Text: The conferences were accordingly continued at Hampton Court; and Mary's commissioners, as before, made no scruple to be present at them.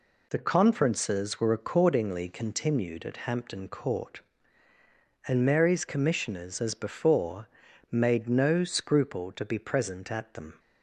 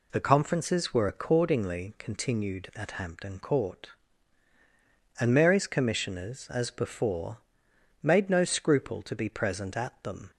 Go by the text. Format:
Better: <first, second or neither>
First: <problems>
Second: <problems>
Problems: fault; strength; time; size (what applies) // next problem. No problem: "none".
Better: neither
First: none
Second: none